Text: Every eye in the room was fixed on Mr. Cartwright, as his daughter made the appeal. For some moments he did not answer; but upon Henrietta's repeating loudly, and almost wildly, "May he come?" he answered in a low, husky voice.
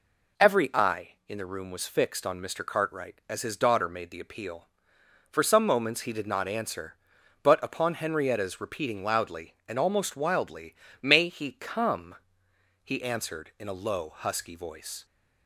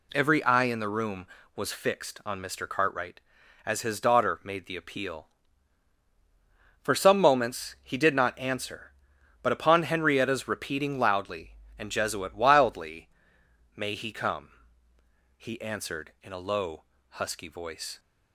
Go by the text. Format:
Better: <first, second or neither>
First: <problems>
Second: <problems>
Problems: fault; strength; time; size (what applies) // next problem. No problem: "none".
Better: first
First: none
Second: says "jesuit" for "almost"; at 11.9 s